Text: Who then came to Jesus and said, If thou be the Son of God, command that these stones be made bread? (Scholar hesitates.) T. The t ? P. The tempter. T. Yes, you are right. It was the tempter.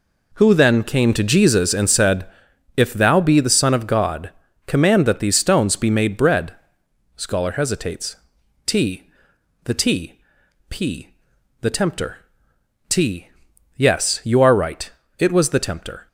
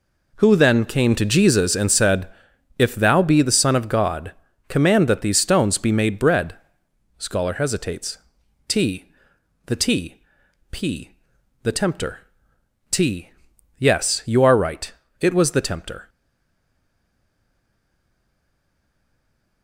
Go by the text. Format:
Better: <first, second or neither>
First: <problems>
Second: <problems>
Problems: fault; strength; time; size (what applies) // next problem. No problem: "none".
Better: first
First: none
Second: stays silent after the last word; strong; from 16.0 s on; 3.6 s long